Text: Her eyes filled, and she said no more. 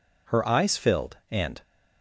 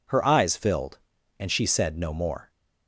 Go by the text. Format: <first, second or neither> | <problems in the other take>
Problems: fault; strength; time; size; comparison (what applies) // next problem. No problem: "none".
second | stops before "she said no more"; at 1.6 s